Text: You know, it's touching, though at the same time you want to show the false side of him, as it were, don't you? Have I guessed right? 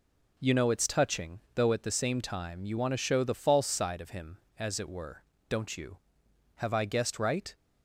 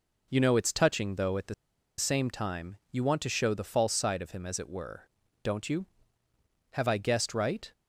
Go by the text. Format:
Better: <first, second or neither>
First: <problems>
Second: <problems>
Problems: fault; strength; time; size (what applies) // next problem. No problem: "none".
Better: first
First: none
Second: pauses between "the" and "same"; at 1.5 s; 0.44 s long